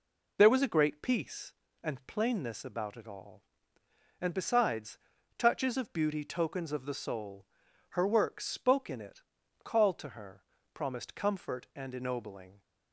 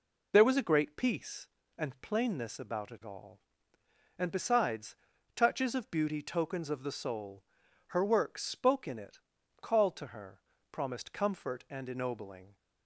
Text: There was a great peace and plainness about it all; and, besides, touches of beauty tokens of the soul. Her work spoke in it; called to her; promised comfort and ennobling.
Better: neither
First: none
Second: none

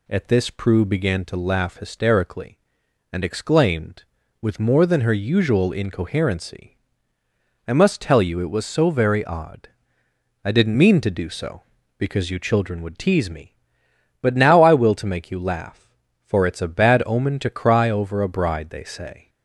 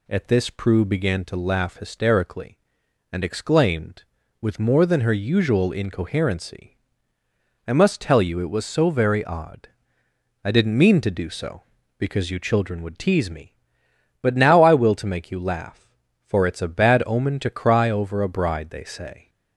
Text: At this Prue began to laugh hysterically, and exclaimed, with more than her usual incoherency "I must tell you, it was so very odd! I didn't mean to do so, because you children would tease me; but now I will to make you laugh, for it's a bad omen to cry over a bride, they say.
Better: neither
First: pauses between "incoherency" and "I"; noticeable; at 6.7 s; 0.90 s long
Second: pauses between "incoherency" and "I"; noticeable; at 6.7 s; 0.90 s long

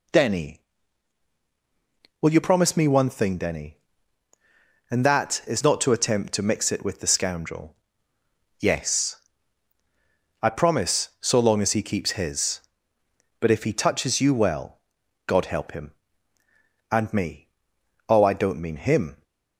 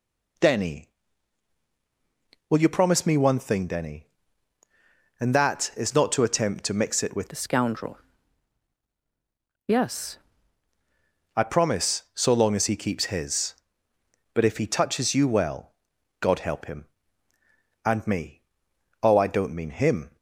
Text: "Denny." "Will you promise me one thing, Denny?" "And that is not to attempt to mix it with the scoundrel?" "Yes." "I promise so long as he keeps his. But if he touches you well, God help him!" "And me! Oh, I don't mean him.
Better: first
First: none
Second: changes voice from "the" to "Yes"; from 7.2 to 10.1 s; 2.9 s long

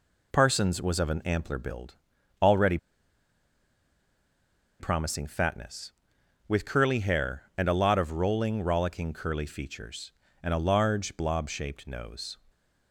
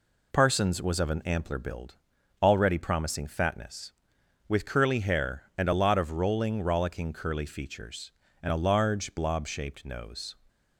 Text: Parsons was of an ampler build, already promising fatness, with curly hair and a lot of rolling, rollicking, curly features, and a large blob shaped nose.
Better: second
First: pauses between "already" and "promising"; strong; at 2.7 s; 2.0 s long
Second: none

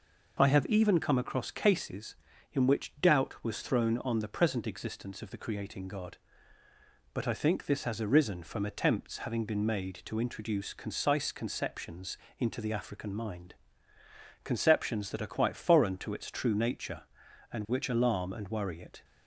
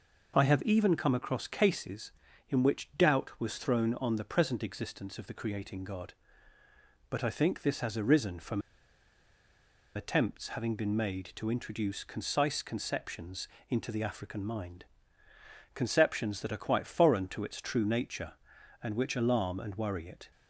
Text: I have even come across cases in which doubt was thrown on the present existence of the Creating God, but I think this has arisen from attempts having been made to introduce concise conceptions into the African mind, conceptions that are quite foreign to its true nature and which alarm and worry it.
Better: first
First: pauses between "conceptions" and "into"; slight; at 12.1 s; 0.22 s long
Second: pauses between "from" and "attempts"; strong; at 8.6 s; 1.3 s long // pauses between "conceptions" and "into"; slight; at 13.4 s; 0.22 s long

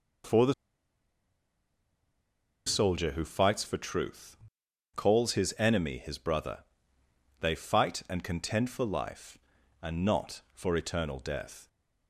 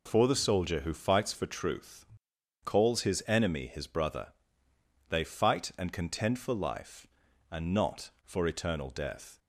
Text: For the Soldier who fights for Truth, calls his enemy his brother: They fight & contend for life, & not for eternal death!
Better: second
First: pauses between "the" and "Soldier"; strong; at 0.5 s; 2.1 s long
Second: none

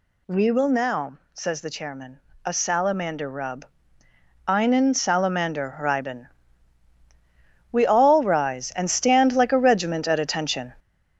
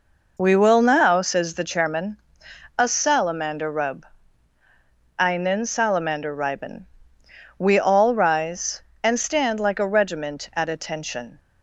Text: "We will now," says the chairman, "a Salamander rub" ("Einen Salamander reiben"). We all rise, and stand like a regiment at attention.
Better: second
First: gets louder; noticeable; throughout; 6 dB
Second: none

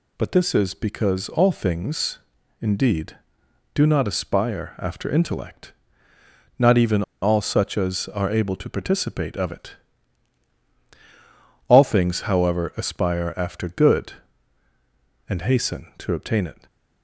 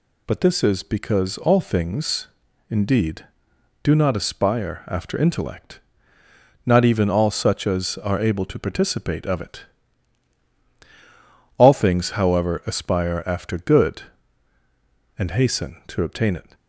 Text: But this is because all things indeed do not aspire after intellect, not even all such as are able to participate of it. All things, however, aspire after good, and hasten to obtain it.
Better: second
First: pauses between "things" and "indeed"; at 2.1 s; 0.42 s long // pauses between "even" and "all"; slight; at 7.0 s; 0.19 s long // stays silent after the last word; slight; from 16.5 s on; 0.5 s long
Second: pauses between "things" and "indeed"; at 2.2 s; 0.42 s long

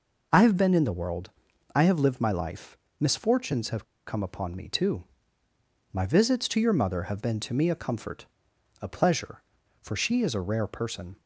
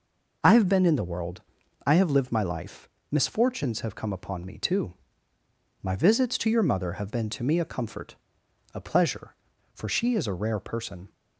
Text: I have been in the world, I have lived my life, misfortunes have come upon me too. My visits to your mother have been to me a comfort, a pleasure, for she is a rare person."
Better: second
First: pauses between "have" and "come"; slight; at 3.8 s; 0.24 s long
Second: none

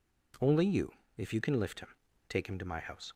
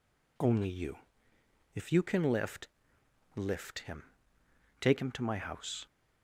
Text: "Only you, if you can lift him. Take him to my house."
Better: first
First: none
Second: says "lift" twice; at 3.3 s

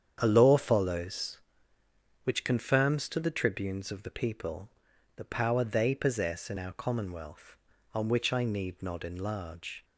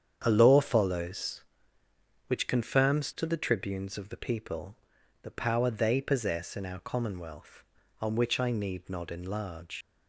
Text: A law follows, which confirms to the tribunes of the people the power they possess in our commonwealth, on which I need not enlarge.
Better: first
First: starts louder than the rest; strong; until 1.2 s; 8 dB // pauses between "people" and "the"; noticeable; at 4.6 s; 0.46 s long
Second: starts louder than the rest; strong; until 1.2 s; 8 dB // pauses between "people" and "the"; noticeable; at 4.7 s; 0.46 s long // leaves "enlarge" unfinished; at 9.8 s; 105 ms

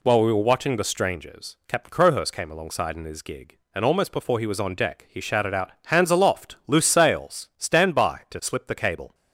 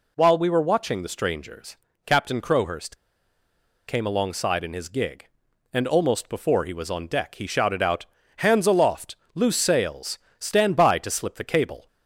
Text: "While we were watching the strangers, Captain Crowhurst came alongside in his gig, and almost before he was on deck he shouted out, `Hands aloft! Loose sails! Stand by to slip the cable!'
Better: first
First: none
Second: pauses between "Crowhurst" and "came"; noticeable; at 2.9 s; 0.90 s long

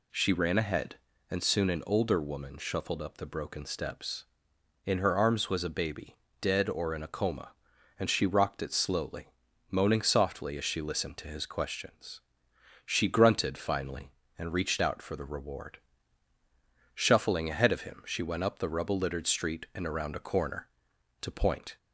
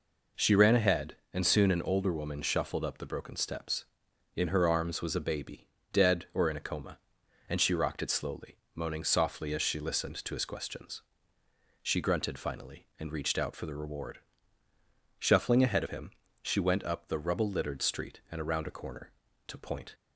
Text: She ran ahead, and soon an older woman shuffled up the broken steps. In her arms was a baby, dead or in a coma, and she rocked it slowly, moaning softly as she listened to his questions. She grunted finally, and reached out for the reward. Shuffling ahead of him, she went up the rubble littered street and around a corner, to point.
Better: neither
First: none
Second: none

